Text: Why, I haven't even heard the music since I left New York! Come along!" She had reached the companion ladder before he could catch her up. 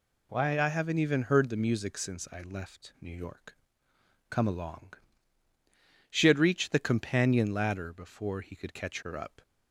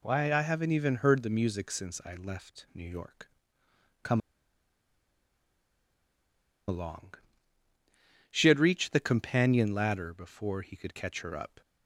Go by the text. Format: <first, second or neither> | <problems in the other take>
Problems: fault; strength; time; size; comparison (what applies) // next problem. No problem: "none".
first | pauses between "Come" and "along"; strong; at 4.1 s; 2.4 s long